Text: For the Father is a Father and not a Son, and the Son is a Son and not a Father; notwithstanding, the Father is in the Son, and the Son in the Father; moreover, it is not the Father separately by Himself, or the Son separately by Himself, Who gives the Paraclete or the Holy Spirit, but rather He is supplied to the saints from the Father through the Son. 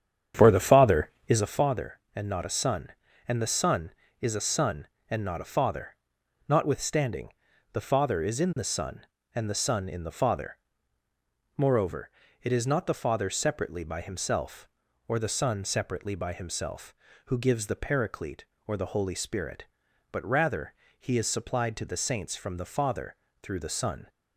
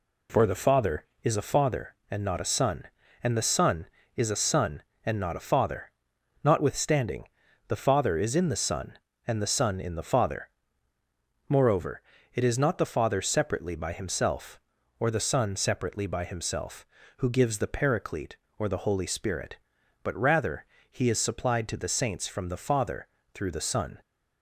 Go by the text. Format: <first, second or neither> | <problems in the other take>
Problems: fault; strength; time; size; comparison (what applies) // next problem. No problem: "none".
second | starts louder than the rest; strong; until 1.6 s; 8.5 dB // pauses between "rather" and "He"; slight; at 20.7 s; 0.28 s long; slight in the second // pauses between "Father" and "through"; slight; at 23.1 s; 0.26 s long; slight in the second